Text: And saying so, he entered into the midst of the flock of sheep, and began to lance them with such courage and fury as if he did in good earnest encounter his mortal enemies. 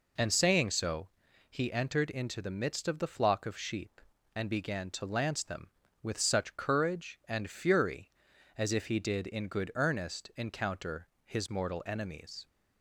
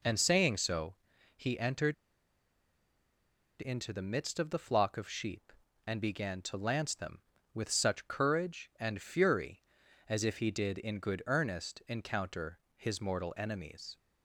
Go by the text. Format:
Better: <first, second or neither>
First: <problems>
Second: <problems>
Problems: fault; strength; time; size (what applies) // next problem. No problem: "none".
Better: first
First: pauses between "encounter" and "his"; slight; at 11.0 s; 0.16 s long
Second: pauses between "entered" and "into"; strong; at 1.9 s; 1.6 s long // pauses between "encounter" and "his"; slight; at 12.5 s; 0.16 s long